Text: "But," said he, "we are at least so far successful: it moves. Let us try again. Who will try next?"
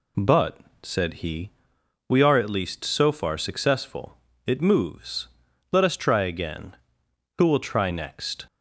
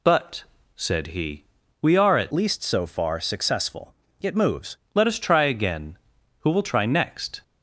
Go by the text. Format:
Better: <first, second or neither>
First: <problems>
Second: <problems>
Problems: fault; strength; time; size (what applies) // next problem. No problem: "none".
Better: first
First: none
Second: changes voice from "least" to "moves"; from 2.3 to 4.7 s; 2.4 s long